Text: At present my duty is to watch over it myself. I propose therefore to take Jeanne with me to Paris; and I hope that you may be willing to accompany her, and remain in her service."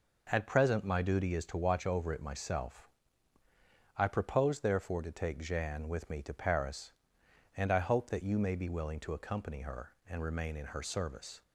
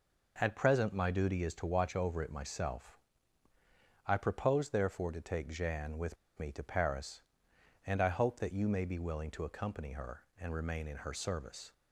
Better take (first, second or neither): first